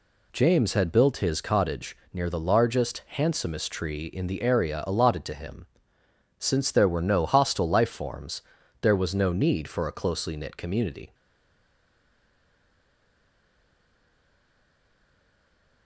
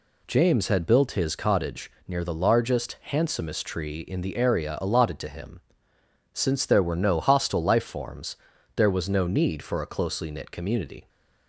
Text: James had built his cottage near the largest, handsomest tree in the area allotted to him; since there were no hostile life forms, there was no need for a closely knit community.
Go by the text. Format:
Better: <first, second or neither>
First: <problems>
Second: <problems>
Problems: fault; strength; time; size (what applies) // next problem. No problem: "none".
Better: second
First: pauses between "cottage" and "near"; slight; at 1.9 s; 0.16 s long // stays silent after the last word; strong; from 11.1 s on; 4.7 s long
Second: pauses between "cottage" and "near"; slight; at 1.9 s; 0.16 s long